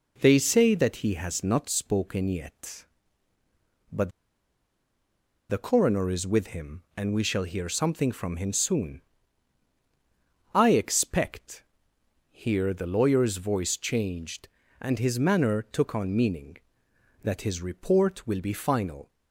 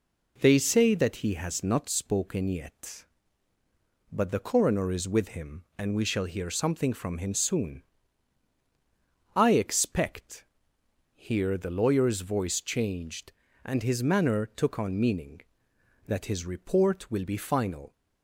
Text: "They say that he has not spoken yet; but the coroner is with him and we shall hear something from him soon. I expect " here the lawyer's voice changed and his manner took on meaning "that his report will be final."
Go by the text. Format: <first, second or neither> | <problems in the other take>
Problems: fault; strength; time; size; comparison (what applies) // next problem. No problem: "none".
second | pauses between "but" and "the"; strong; at 4.1 s; 1.3 s long